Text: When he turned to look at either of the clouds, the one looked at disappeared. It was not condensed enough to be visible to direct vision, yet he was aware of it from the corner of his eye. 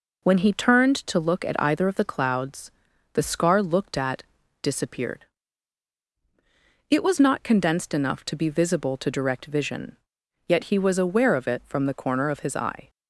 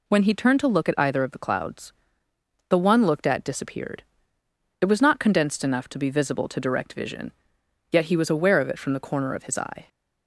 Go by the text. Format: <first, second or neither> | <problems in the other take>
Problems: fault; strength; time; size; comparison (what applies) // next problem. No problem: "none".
second | says "scar" for "one"; at 3.2 s // pauses between "at" and "disappeared"; at 4.2 s; 0.38 s long